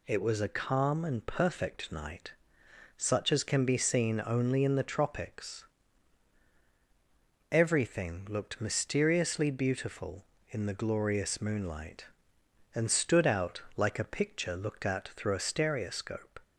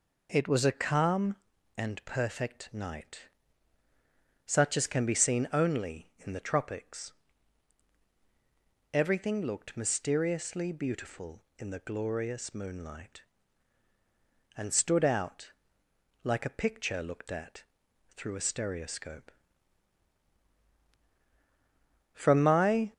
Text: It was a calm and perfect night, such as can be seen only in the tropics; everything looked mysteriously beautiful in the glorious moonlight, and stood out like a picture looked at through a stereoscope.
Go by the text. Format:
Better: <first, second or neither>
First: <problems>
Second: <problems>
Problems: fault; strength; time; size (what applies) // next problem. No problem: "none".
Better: first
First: pauses between "out" and "like"; slight; at 13.6 s; 0.16 s long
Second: pauses between "out" and "like"; noticeable; at 15.5 s; 0.72 s long // pauses between "at" and "through"; noticeable; at 17.6 s; 0.50 s long // goes on to say "From my"; noticeable; from 22.1 s on; 0.80 s long